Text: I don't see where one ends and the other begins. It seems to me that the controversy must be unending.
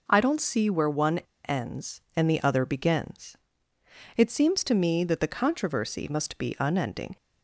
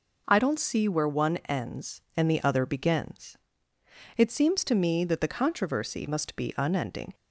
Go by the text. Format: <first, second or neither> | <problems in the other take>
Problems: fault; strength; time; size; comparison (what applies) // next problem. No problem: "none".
second | pauses between "one" and "ends"; slight; at 1.1 s; 0.30 s long